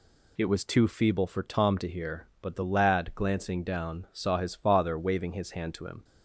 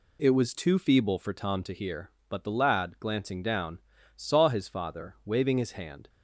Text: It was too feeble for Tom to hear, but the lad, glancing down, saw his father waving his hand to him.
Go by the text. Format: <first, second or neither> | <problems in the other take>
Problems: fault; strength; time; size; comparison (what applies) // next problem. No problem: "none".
first | stops before "to him"; at 6.0 s